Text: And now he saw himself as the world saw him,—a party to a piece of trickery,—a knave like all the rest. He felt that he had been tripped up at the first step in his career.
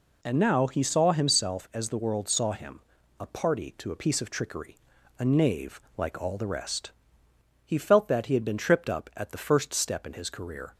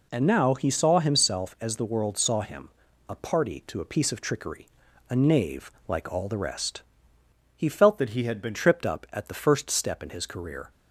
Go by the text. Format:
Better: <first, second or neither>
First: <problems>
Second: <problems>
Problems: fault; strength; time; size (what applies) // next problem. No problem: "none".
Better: first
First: pauses between "knave" and "like"; slight; at 5.7 s; 0.16 s long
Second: pauses between "knave" and "like"; slight; at 5.7 s; 0.16 s long // changes voice from "that" to "been"; from 7.9 to 8.5 s; 0.6 s long